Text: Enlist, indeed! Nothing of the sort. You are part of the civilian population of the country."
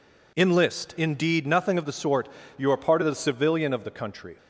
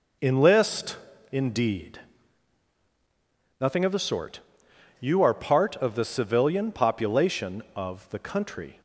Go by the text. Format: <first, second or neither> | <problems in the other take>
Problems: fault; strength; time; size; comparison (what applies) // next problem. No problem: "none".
second | skips "population"; at 3.7 s